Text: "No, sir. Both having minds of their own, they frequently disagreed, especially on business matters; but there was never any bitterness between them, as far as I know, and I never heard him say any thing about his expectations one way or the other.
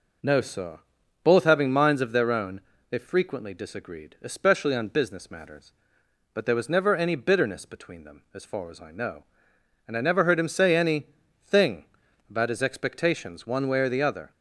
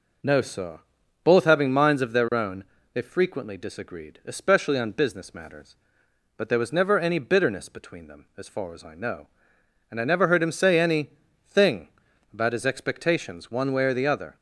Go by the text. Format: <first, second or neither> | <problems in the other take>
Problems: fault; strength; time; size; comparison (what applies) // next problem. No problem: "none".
neither | pauses between "any" and "thing"; the same in both // pauses between "thing" and "about"; noticeable; the same in both